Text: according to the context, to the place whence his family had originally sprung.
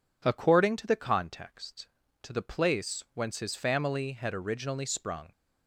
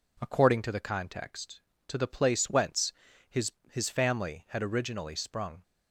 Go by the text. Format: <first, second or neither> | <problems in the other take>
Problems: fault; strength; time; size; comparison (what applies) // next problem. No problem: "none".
first | pauses between "whence" and "his"; slight; at 2.9 s; 0.36 s long // says "his" twice; at 3.7 s